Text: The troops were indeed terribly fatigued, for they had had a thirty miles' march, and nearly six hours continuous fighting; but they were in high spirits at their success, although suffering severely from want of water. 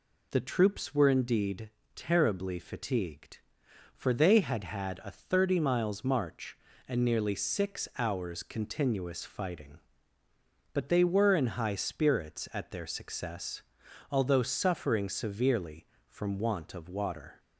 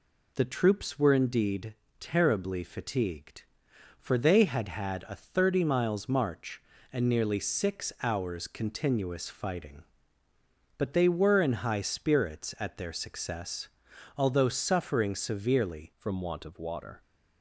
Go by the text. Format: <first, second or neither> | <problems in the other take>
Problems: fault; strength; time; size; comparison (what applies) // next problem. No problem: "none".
first | pauses between "indeed" and "terribly"; slight; at 1.7 s; 0.26 s long; slight in the first // changes voice at "from"; from 15.9 s on; 1.1 s long